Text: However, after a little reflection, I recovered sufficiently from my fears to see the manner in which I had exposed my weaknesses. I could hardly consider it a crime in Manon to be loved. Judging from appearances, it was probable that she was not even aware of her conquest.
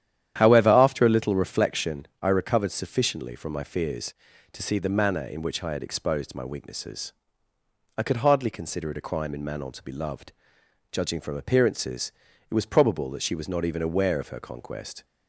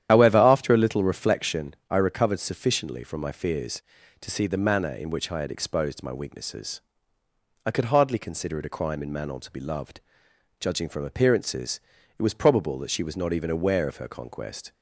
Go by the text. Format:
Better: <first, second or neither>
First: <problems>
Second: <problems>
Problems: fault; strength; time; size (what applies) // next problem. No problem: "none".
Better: first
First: starts louder than the rest; strong; until 1.3 s; 10.5 dB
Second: loses the start of "However"; at 0.0 s; 60 ms // starts louder than the rest; strong; until 1.1 s; 10.5 dB